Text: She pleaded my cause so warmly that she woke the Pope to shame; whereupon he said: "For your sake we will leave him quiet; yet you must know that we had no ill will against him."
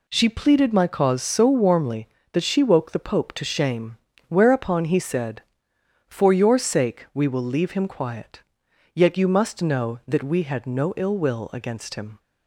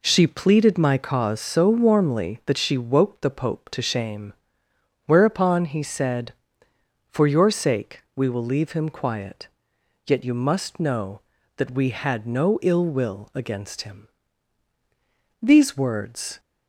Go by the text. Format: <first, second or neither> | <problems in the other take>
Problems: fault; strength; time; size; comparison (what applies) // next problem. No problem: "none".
first | goes on to say "These words"; noticeable; from 15.4 s on; 0.98 s long